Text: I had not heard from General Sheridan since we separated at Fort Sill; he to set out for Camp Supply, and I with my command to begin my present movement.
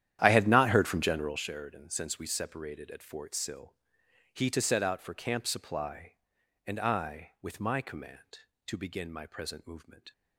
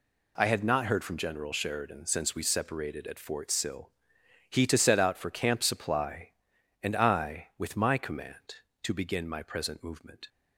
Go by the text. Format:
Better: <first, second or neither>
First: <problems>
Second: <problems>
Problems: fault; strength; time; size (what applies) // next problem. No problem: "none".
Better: second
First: starts louder than the rest; strong; until 1.4 s; 11 dB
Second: none